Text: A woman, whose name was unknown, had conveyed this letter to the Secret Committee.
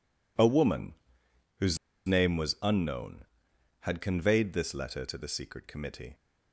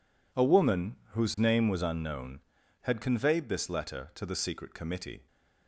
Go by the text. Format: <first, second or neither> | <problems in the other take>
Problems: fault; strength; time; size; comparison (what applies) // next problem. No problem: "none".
second | pauses between "whose" and "name"; slight; at 1.7 s; 0.31 s long